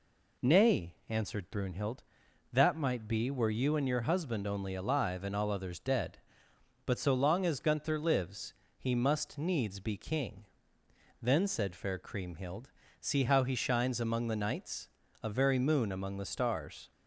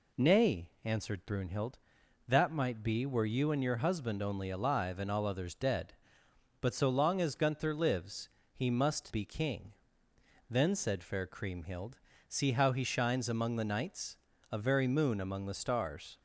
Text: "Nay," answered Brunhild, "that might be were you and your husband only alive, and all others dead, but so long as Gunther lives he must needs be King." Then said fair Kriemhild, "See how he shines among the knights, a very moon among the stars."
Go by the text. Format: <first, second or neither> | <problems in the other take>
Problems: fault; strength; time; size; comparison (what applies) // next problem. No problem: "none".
first | pauses between "lives" and "he"; slight; at 8.2 s; 0.24 s long; slight in the first // skips "needs"; at 9.1 s